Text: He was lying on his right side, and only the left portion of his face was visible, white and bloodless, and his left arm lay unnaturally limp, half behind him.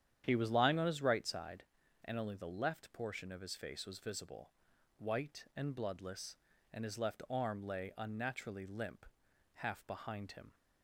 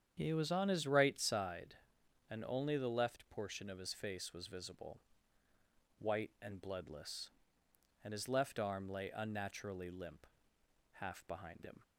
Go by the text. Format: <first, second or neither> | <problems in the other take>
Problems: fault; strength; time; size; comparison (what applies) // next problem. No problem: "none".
first | starts louder than the rest; strong; until 1.1 s; 8.5 dB; strong in the first // skips "lying"; at 0.5 s